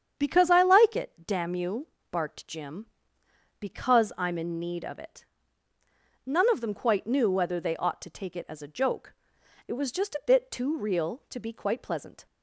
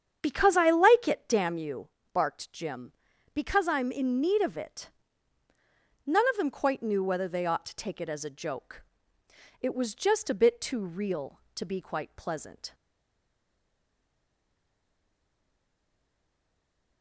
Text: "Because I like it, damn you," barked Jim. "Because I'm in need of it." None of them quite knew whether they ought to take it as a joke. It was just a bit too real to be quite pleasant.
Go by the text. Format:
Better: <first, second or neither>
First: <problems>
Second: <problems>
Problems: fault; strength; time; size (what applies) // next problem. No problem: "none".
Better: first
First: starts louder than the rest; strong; until 1.2 s; 8 dB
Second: starts louder than the rest; strong; until 1.2 s; 8 dB // stays silent after the last word; strong; from 12.7 s on; 4.3 s long